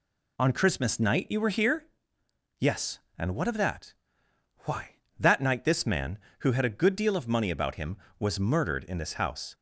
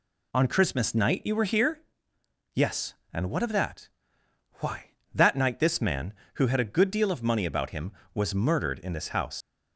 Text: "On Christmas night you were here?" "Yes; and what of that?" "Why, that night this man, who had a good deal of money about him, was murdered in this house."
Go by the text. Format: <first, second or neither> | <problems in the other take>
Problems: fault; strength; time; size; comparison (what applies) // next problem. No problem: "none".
first | leaves "house" unfinished; at 9.4 s; 85 ms